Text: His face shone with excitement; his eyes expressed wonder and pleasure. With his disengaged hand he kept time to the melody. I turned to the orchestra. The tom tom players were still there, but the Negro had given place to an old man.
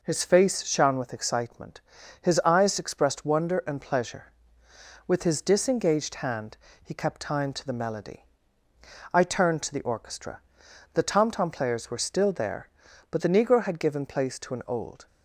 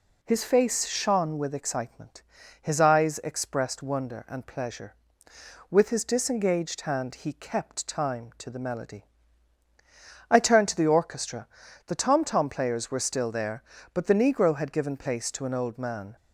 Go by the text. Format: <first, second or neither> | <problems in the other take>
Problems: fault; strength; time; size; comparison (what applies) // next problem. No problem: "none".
second | pauses between "hand" and "he"; slight; at 6.5 s; 0.26 s long // stops before "man"; at 15.0 s